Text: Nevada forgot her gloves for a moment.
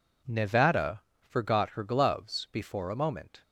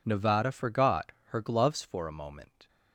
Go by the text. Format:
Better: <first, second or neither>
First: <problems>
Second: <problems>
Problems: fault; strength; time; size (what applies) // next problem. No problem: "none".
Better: second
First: pauses between "Nevada" and "forgot"; slight; at 1.0 s; 0.24 s long // says "before" for "for"; at 2.5 s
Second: none